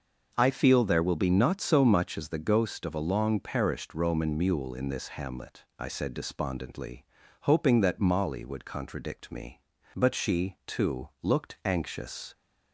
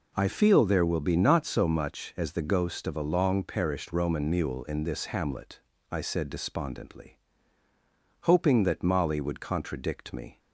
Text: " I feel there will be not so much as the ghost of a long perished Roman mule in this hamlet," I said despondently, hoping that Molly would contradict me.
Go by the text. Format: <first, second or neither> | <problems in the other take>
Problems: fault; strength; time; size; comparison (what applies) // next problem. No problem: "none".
second | goes on to say "But she too looked anxious"; strong; from 9.9 s on; 2.3 s long